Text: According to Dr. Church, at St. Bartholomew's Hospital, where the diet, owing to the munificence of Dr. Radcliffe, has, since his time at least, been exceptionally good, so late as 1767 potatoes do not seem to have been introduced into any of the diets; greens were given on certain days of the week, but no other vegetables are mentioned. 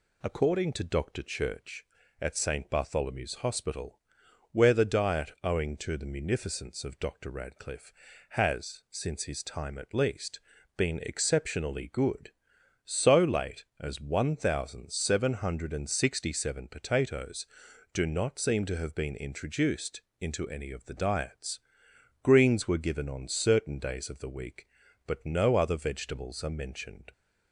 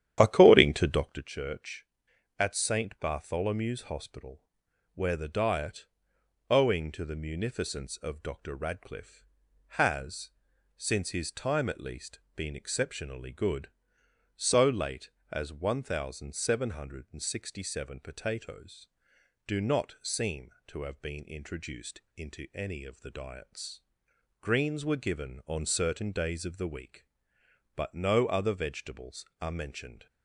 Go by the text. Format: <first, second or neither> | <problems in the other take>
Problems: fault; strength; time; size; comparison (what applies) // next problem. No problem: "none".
first | starts louder than the rest; strong; until 1.3 s; 10.5 dB // pauses between "introduced" and "into"; slight; at 22.0 s; 0.15 s long; slight in the first